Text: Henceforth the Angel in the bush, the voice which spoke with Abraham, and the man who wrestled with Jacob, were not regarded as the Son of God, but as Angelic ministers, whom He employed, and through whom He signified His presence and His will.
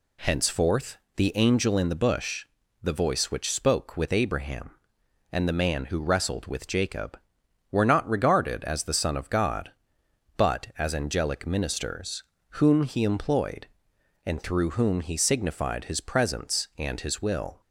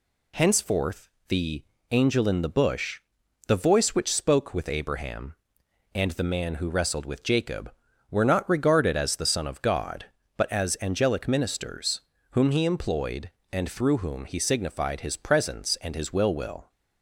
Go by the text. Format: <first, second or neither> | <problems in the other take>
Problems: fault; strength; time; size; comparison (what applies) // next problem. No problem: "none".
first | pauses between "Henceforth" and "the"; slight; at 1.0 s; 0.22 s long; slight in the first // pauses between "the" and "Angel"; slight; at 1.6 s; 0.28 s long // says "will" twice; at 16.3 s